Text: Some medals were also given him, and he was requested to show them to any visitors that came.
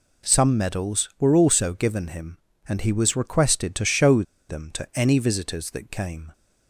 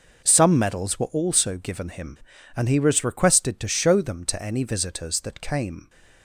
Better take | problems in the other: second | pauses between "show" and "them"; slight; at 4.2 s; 0.27 s long

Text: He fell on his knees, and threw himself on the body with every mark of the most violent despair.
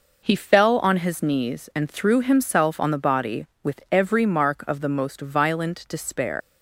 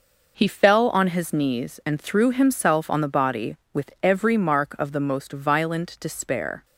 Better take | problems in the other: second | leaves "despair" unfinished; at 6.4 s; 130 ms

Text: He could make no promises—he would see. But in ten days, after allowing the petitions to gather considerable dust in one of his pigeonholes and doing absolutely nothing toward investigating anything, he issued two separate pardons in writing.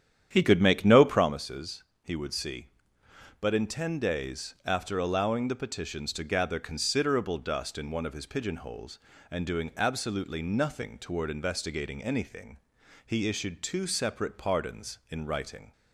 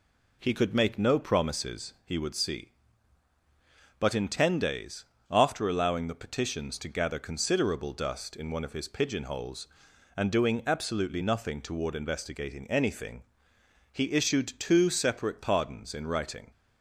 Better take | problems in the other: second | starts louder than the rest; strong; until 1.3 s; 9.5 dB

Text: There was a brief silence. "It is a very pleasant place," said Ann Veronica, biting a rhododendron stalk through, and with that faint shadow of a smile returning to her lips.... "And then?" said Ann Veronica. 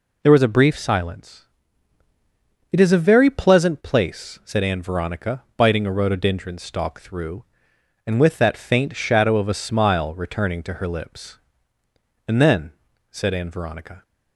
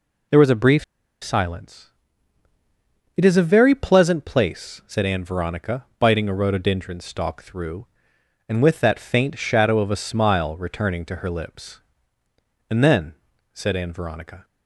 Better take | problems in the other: first | pauses between "brief" and "silence"; at 0.8 s; 0.38 s long

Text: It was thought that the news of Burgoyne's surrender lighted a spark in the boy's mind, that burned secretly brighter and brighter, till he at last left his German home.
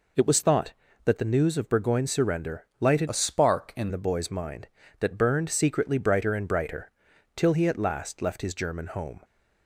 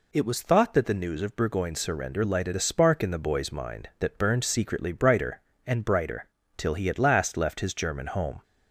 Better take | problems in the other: second | changes voice from "a" to "in"; from 3.0 to 3.8 s; 0.8 s long

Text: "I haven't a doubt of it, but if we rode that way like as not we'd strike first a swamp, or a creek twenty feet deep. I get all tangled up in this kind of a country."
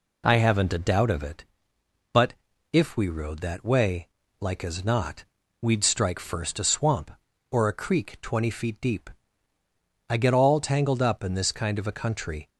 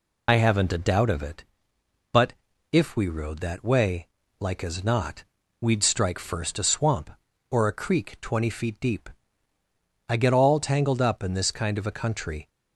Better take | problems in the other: first | loses the start of "I"; at 0.2 s; 50 ms // pauses between "but" and "if"; at 2.3 s; 0.40 s long; also in the first // pauses between "way" and "like"; slight; at 4.0 s; 0.34 s long; slight in the first // pauses between "not" and "we'd"; at 5.2 s; 0.38 s long; also in the first

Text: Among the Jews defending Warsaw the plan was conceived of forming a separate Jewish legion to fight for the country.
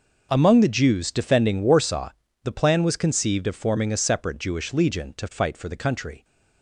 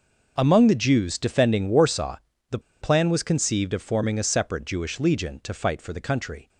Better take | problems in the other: first | pauses between "Warsaw" and "the"; slight; at 2.1 s; 0.34 s long; slight in the first // pauses between "the" and "plan"; slight; at 2.5 s; 0.22 s long

